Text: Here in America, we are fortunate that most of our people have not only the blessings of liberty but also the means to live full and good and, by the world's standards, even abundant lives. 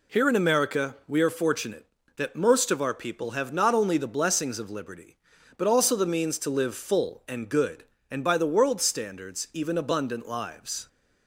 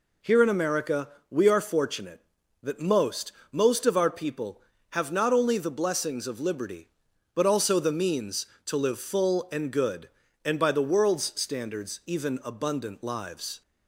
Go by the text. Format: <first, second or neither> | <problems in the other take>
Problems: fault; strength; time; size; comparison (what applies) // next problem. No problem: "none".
first | says "most" twice; at 3.5 s